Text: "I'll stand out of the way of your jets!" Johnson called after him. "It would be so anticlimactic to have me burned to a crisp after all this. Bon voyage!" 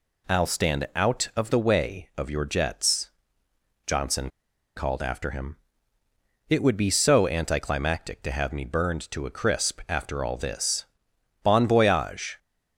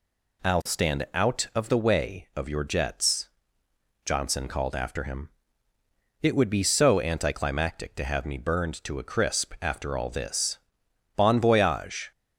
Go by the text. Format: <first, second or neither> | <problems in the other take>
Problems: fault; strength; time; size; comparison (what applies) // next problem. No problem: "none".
second | pauses between "Johnson" and "called"; at 4.3 s; 0.45 s long